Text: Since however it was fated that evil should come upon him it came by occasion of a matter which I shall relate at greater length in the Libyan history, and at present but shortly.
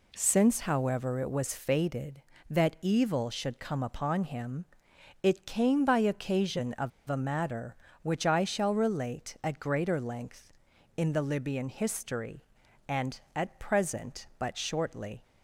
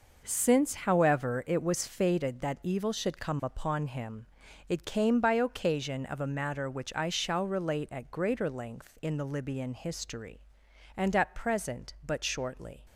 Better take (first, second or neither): second